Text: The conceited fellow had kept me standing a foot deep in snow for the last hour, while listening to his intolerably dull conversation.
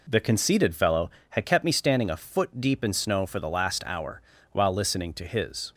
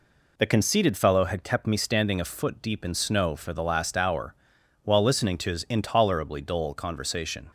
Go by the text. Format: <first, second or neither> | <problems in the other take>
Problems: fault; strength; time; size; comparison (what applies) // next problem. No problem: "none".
second | stops before "intolerably dull conversation"; at 5.7 s